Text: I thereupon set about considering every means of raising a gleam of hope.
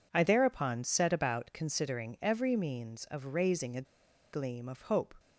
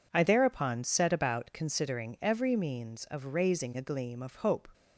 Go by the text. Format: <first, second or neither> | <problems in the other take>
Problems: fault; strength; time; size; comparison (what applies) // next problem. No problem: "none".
second | pauses between "a" and "gleam"; noticeable; at 3.8 s; 0.49 s long